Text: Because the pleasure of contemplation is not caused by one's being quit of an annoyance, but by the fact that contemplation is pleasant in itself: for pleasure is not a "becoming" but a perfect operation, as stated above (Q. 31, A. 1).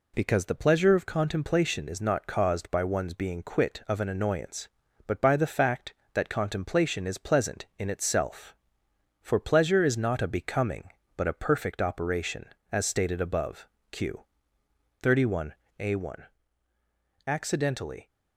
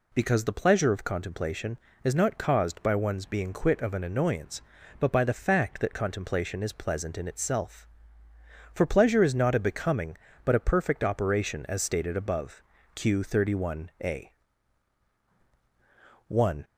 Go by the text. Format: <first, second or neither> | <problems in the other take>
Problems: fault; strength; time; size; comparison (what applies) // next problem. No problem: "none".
second | goes on to say "Accidentally"; noticeable; from 17.2 s on; 0.82 s long